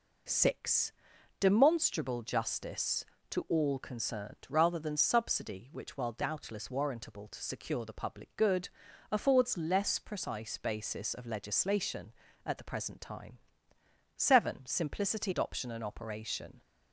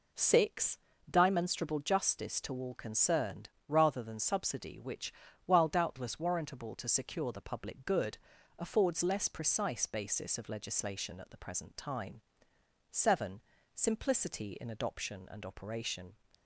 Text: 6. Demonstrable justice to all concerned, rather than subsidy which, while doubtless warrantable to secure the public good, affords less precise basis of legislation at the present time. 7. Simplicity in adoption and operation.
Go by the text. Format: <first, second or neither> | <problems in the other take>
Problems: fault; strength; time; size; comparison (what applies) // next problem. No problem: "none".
second | skips "in"; at 15.3 s